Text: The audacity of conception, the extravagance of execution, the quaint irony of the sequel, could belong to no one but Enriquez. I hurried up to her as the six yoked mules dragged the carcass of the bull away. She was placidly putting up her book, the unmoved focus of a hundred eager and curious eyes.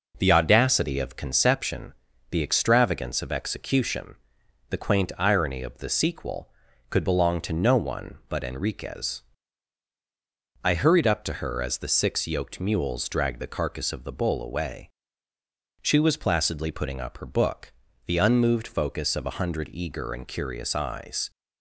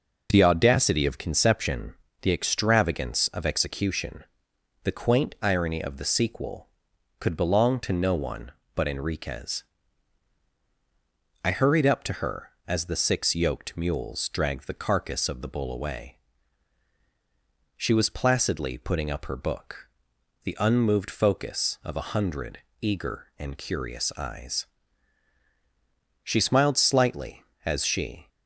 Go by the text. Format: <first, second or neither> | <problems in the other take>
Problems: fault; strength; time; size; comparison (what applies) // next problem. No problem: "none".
first | pauses between "hundred" and "eager"; slight; at 22.5 s; 0.22 s long // goes on to say "She smiled slightly as she"; strong; from 26.2 s on; 2.0 s long